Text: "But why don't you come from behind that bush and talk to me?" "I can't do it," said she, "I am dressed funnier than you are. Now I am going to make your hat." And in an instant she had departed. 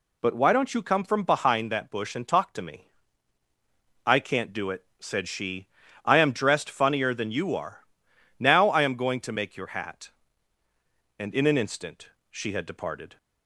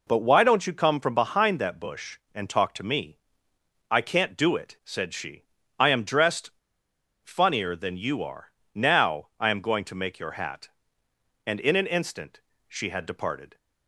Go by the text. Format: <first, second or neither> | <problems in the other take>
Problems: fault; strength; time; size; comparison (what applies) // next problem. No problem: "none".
first | pauses between "dressed" and "funnier"; noticeable; at 6.4 s; 0.74 s long // pauses between "instant" and "she"; slight; at 12.3 s; 0.30 s long; slight in the first